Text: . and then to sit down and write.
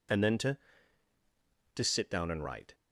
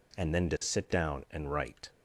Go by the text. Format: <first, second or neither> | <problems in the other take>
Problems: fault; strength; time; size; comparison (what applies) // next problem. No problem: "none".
second | says "to" twice; at 1.7 s